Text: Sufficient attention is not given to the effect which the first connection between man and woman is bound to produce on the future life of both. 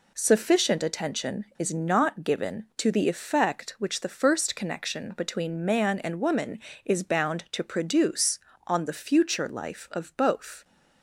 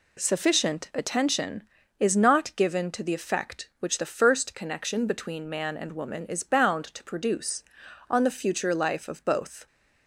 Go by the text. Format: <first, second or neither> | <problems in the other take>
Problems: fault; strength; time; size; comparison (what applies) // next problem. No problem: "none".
neither | none